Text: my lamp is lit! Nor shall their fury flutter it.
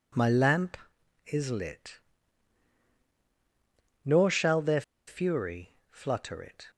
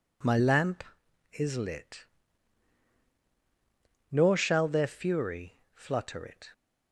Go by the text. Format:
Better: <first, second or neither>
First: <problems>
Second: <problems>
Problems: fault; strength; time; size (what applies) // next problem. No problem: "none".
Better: second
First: pauses between "their" and "fury"; slight; at 4.8 s; 0.25 s long // pauses between "fury" and "flutter"; slight; at 5.7 s; 0.18 s long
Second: pauses between "fury" and "flutter"; slight; at 5.5 s; 0.18 s long